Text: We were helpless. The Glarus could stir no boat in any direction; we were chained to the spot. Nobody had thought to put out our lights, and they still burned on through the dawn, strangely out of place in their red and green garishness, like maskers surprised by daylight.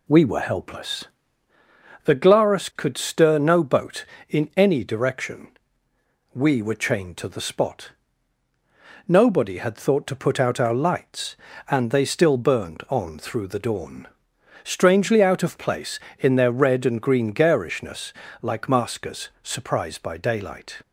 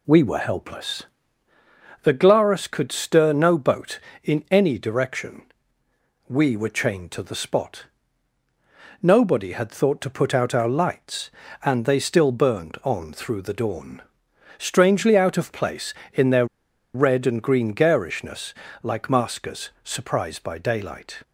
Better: first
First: pauses between "maskers" and "surprised"; slight; at 19.2 s; 0.16 s long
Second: pauses between "their" and "red"; noticeable; at 16.4 s; 0.49 s long // pauses between "maskers" and "surprised"; slight; at 19.6 s; 0.16 s long

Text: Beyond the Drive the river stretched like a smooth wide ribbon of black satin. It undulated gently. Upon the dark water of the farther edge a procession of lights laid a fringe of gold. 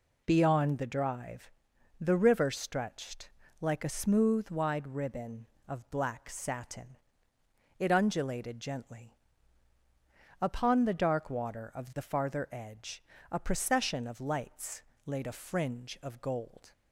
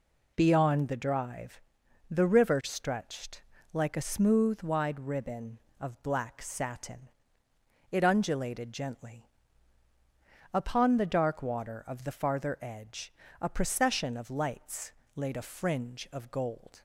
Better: neither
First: pauses between "Drive" and "the"; noticeable; at 1.5 s; 0.48 s long // pauses between "stretched" and "like"; slight; at 3.2 s; 0.30 s long // pauses between "edge" and "a"; slight; at 13.0 s; 0.26 s long // pauses between "lights" and "laid"; slight; at 14.8 s; 0.24 s long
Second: pauses between "Drive" and "the"; noticeable; at 1.6 s; 0.48 s long // pauses between "stretched" and "like"; slight; at 3.4 s; 0.30 s long // pauses between "edge" and "a"; slight; at 13.1 s; 0.26 s long // pauses between "lights" and "laid"; slight; at 14.9 s; 0.24 s long

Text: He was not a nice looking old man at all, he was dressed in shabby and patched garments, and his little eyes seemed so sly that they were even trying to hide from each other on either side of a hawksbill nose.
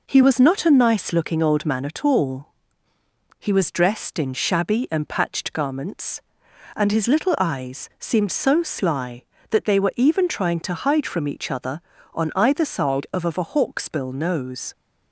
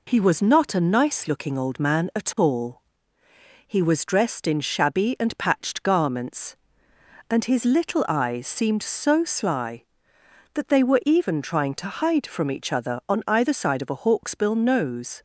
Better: second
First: says "of" twice; at 13.2 s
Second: none

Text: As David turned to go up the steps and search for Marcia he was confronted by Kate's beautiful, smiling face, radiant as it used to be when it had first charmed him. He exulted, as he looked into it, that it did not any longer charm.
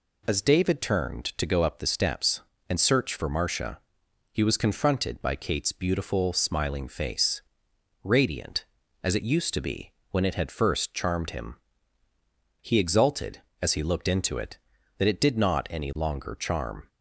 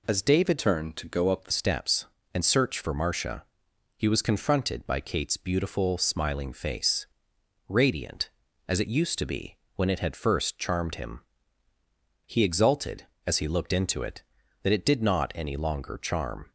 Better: first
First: pauses between "Marcia" and "he"; noticeable; at 3.7 s; 0.54 s long // pauses between "be" and "when"; slight; at 9.9 s; 0.20 s long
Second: changes voice from "turned" to "the"; from 0.5 to 1.5 s; 1.0 s long // pauses between "Marcia" and "he"; noticeable; at 3.4 s; 0.54 s long // pauses between "be" and "when"; slight; at 9.5 s; 0.20 s long

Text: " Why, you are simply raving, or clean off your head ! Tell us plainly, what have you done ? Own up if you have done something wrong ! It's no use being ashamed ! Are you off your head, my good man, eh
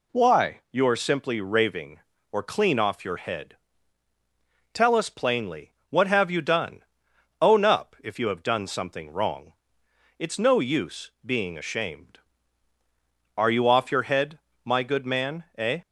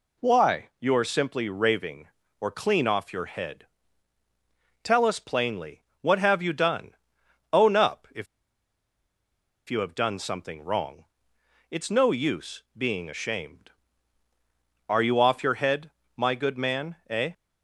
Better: first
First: none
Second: pauses between "if" and "you"; strong; at 8.2 s; 1.4 s long

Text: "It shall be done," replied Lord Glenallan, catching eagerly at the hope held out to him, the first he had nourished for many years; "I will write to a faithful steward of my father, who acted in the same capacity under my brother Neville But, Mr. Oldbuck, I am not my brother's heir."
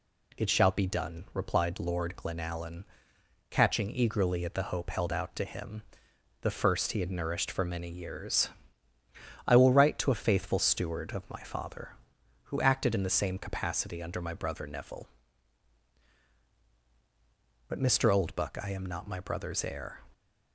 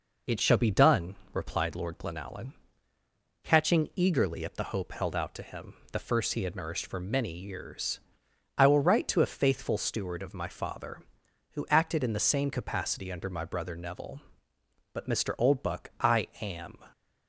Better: first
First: none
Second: stops before "not my brother's heir"; at 16.9 s

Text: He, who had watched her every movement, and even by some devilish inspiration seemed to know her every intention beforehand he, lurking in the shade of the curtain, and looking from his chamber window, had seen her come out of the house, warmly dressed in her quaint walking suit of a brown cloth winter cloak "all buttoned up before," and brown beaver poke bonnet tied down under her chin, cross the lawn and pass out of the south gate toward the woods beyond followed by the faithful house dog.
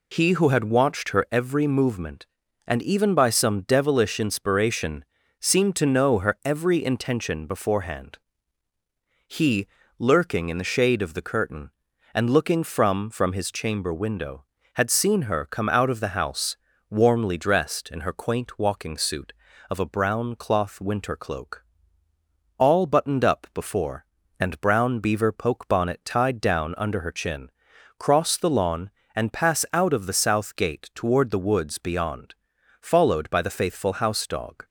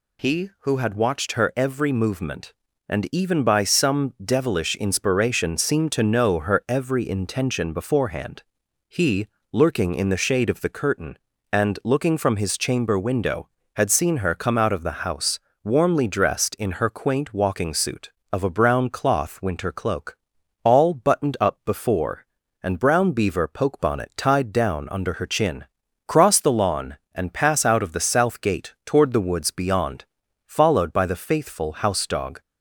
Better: second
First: pauses between "inspiration" and "seemed"; slight; at 5.0 s; 0.34 s long // pauses between "beforehand" and "he"; at 8.1 s; 1.0 s long // says "from" twice; at 13.0 s // pauses between "cloak" and "all"; noticeable; at 21.6 s; 0.94 s long // pauses between "beyond" and "followed"; noticeable; at 32.3 s; 0.46 s long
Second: pauses between "beforehand" and "he"; at 8.4 s; 0.44 s long // pauses between "cloak" and "all"; noticeable; at 20.1 s; 0.46 s long // pauses between "beyond" and "followed"; noticeable; at 30.0 s; 0.56 s long

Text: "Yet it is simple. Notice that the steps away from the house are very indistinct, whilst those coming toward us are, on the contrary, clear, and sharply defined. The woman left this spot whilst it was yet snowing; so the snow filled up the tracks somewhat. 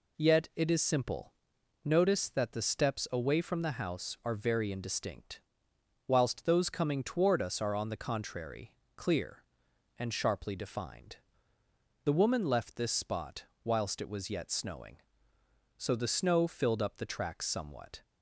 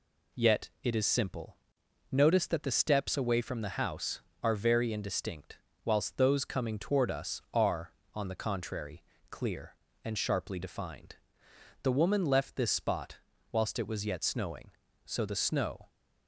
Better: first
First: pauses between "spot" and "whilst"; slight; at 13.4 s; 0.20 s long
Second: pauses between "spot" and "whilst"; slight; at 13.1 s; 0.32 s long // stops before "filled up the tracks somewhat"; at 15.8 s

